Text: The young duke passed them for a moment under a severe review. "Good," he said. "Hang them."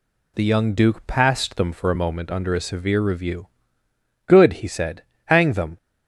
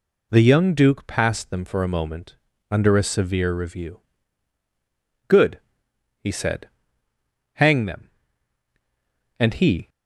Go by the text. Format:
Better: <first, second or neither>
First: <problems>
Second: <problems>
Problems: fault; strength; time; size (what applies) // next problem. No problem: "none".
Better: first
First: none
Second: pauses between "moment" and "under"; slight; at 2.3 s; 0.34 s long // goes on to say "And he"; from 9.3 s on; 0.50 s long